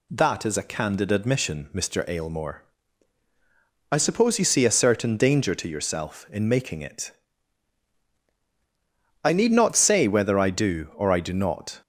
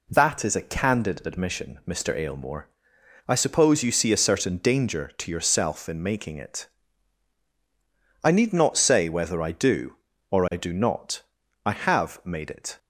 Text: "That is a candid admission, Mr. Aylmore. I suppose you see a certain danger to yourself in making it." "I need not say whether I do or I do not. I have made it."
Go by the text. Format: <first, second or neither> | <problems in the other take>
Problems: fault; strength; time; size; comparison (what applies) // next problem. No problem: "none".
second | stops before "I have made it"; at 11.8 s